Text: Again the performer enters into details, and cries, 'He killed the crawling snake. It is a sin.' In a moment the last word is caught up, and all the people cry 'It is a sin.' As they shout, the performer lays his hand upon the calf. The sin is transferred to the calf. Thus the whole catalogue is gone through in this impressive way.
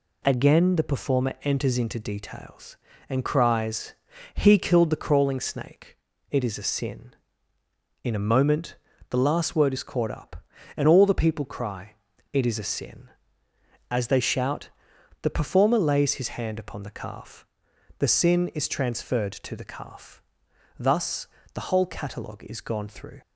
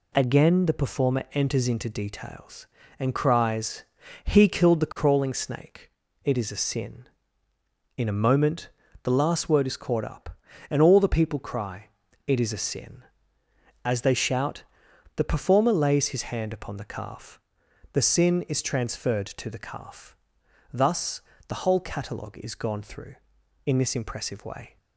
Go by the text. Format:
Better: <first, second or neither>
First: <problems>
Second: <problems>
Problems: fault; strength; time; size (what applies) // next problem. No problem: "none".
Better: second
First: pauses between "moment" and "the"; slight; at 8.7 s; 0.34 s long // pauses between "cry" and "It"; slight; at 11.9 s; 0.36 s long // pauses between "Thus" and "the"; slight; at 21.2 s; 0.26 s long // stops before "in this impressive way"; at 23.2 s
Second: pauses between "moment" and "the"; slight; at 8.6 s; 0.34 s long // pauses between "cry" and "It"; slight; at 11.8 s; 0.36 s long // pauses between "Thus" and "the"; slight; at 21.2 s; 0.26 s long